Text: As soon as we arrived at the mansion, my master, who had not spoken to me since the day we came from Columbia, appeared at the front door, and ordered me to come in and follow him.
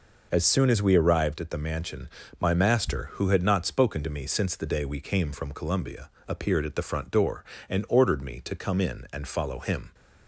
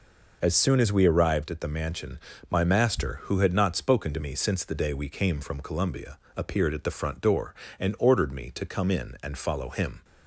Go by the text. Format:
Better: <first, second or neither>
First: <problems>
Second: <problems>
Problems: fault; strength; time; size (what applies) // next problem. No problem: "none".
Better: neither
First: none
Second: none